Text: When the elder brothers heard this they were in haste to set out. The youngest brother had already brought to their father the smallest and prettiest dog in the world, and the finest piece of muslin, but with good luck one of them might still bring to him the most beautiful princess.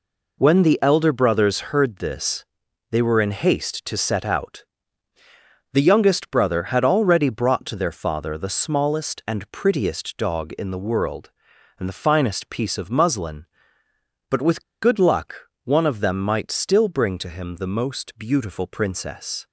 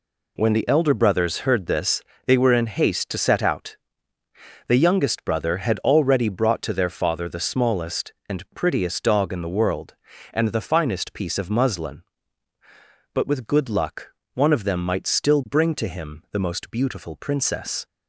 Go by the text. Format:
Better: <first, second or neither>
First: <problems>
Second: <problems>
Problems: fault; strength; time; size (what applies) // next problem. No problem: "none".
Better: second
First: pauses between "this" and "they"; noticeable; at 2.4 s; 0.48 s long // pauses between "with" and "good"; slight; at 14.6 s; 0.19 s long // pauses between "luck" and "one"; slight; at 15.4 s; 0.24 s long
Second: pauses between "this" and "they"; slight; at 2.0 s; 0.24 s long // pauses between "luck" and "one"; slight; at 14.0 s; 0.26 s long